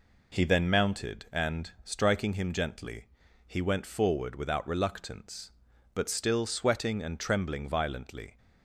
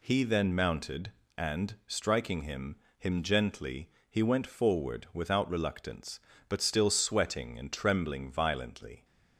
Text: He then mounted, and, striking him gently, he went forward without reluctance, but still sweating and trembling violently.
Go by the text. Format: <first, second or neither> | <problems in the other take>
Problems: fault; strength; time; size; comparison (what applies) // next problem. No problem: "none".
first | says "him" twice; at 2.9 s